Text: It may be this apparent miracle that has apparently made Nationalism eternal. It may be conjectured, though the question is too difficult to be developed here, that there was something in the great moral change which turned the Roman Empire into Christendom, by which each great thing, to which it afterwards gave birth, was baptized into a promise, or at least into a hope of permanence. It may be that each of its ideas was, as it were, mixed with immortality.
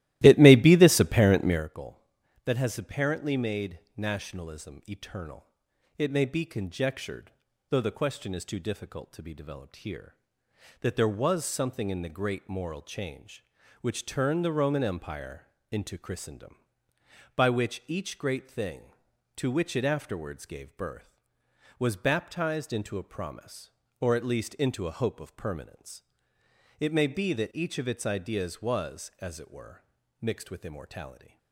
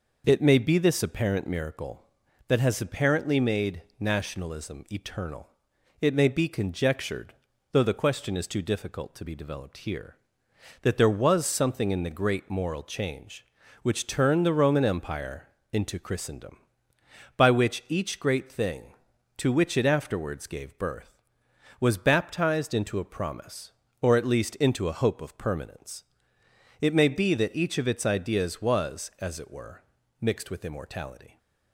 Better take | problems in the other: second | starts louder than the rest; strong; until 1.7 s; 16 dB // pauses between "Empire" and "into"; slight; at 15.4 s; 0.24 s long; slight in the second

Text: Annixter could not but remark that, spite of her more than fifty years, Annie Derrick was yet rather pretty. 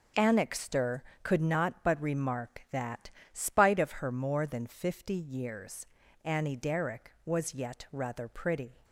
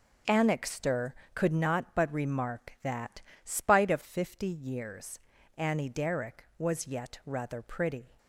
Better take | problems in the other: first | starts louder than the rest; until 1.5 s; 6.5 dB; also in the first // skips "her more than"; at 4.0 s

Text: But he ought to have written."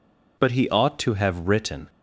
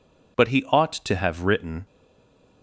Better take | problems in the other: first | stays silent after the last word; slight; from 1.8 s on; 0.8 s long

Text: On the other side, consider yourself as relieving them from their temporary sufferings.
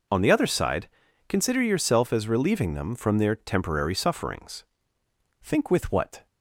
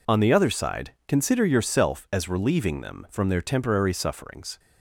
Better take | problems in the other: second | goes on to say "Think with what"; noticeable; from 5.4 s on; 0.84 s long

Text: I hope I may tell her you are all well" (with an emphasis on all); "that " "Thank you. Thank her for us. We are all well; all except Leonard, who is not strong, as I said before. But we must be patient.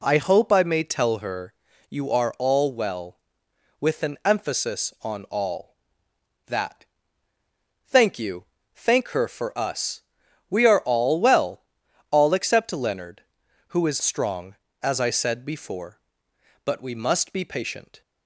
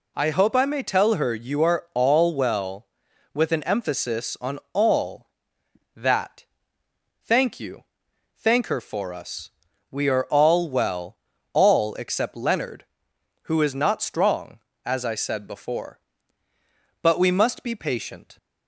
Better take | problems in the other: second | pauses between "her" and "you"; slight; at 1.5 s; 0.34 s long // skips "not"; at 14.0 s

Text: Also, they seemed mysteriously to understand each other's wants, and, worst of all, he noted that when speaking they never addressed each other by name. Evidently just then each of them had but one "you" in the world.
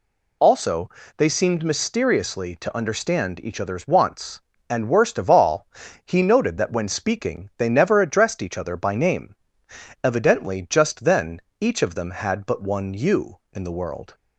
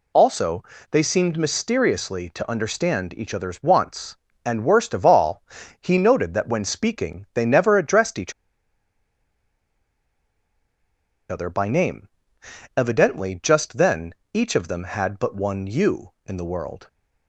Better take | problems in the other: first | pauses between "each" and "other"; strong; at 8.3 s; 2.9 s long // pauses between "then" and "each"; slight; at 14.1 s; 0.22 s long; slight in the first

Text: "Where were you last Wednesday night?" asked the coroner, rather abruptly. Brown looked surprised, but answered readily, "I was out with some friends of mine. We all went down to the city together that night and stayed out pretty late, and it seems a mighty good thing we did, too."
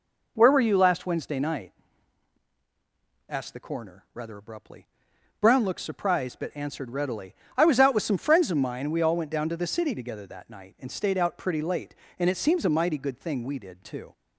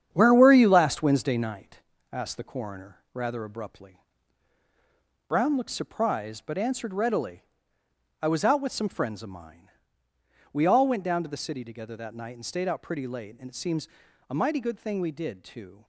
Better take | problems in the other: first | gets quieter; strong; throughout; 7 dB // pauses between "seems" and "a"; at 13.8 s; 0.42 s long

